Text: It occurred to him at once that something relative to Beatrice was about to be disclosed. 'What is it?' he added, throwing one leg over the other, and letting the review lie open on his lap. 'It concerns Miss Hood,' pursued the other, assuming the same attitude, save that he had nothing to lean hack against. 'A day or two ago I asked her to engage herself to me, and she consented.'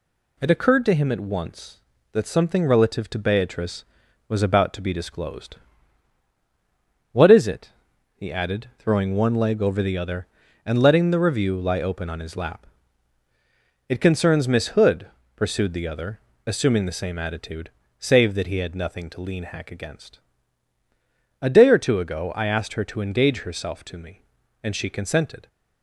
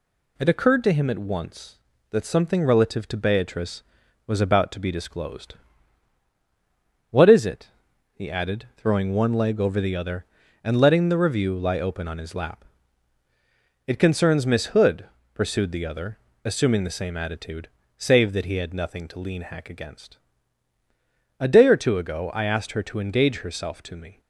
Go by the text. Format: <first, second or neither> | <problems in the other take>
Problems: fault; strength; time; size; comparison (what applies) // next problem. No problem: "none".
first | stops before "and she consented"; at 24.1 s